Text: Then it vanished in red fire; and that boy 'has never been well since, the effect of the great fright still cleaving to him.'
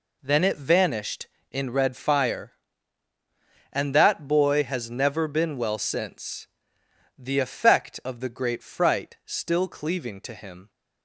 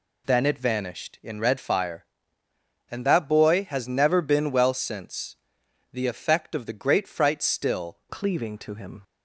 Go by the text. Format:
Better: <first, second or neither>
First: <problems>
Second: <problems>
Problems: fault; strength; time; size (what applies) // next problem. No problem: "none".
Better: first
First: none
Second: changes voice at "cleaving"; from 8.0 s on; 1.0 s long